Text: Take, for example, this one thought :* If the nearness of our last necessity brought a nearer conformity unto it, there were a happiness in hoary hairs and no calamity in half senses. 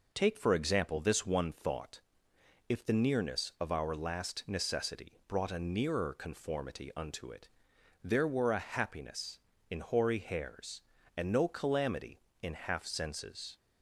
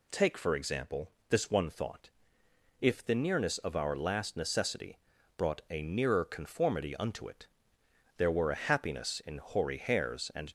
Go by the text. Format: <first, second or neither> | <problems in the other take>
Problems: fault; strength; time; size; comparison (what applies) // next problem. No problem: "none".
first | pauses between "necessity" and "brought"; at 4.9 s; 0.38 s long // stops before "no calamity in half senses"; at 10.4 s